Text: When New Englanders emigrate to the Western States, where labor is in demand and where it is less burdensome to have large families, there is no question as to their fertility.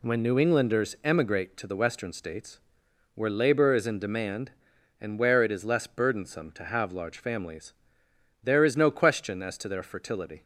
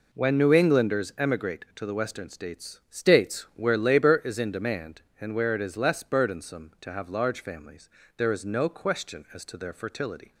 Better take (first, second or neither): first